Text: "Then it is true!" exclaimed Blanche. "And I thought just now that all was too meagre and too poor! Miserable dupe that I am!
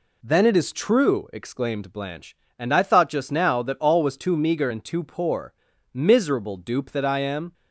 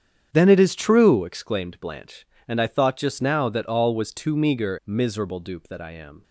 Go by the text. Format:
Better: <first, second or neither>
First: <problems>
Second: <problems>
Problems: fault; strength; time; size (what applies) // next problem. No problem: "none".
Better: first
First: none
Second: starts louder than the rest; strong; until 1.3 s; 8.5 dB // skips "and too poor"; at 4.8 s